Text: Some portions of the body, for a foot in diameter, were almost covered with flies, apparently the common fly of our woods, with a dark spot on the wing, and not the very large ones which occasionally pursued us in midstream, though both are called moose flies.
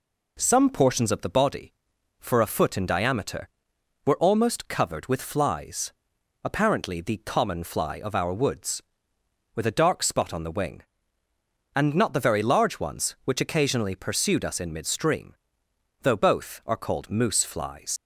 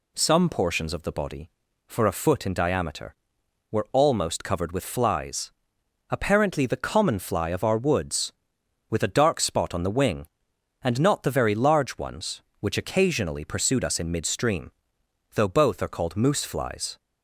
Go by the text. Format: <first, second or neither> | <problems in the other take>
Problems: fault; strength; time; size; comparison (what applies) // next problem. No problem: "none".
second | leaves "flies" unfinished; at 17.9 s; 95 ms